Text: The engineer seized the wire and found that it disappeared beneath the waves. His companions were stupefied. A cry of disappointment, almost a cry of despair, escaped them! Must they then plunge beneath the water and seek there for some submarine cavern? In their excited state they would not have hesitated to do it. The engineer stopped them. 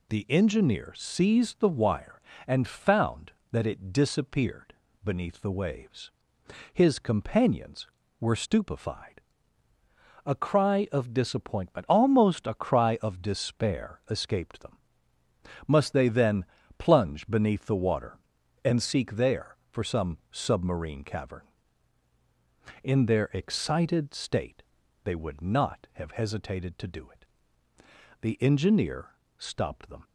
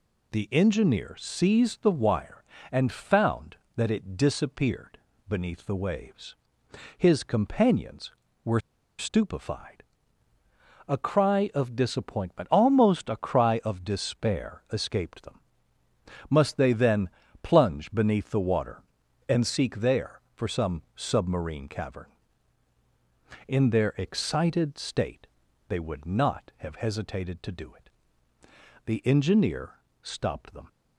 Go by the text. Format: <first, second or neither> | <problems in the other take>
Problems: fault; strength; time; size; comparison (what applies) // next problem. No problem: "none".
first | pauses between "disappeared" and "beneath"; slight; at 4.9 s; 0.30 s long; slight in the first // pauses between "were" and "stupefied"; at 8.5 s; 0.38 s long // pauses between "then" and "plunge"; slight; at 17.0 s; 0.32 s long; slight in the first // pauses between "state" and "they"; at 25.2 s; 0.42 s long; also in the first // pauses between "engineer" and "stopped"; slight; at 29.7 s; 0.32 s long; slight in the first